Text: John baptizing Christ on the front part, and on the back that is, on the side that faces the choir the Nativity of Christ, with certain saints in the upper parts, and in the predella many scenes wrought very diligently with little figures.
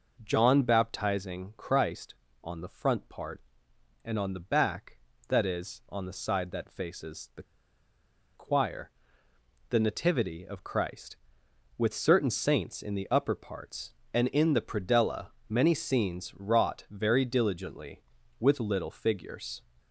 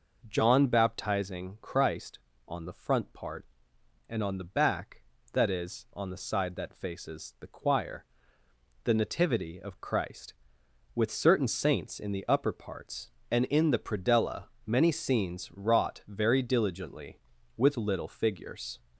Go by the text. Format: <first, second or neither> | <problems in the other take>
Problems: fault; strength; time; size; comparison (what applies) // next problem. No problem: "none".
second | pauses between "the" and "choir"; noticeable; at 7.4 s; 0.91 s long // pauses between "choir" and "the"; noticeable; at 8.9 s; 0.78 s long; noticeable in the second // pauses between "predella" and "many"; slight; at 15.2 s; 0.22 s long; slight in the second